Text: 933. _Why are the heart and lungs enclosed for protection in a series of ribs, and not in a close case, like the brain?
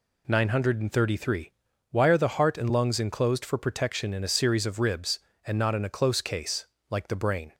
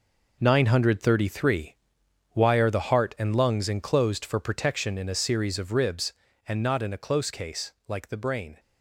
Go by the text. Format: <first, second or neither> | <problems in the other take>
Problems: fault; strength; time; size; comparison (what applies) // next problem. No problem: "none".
first | gets quieter; strong; throughout; 9 dB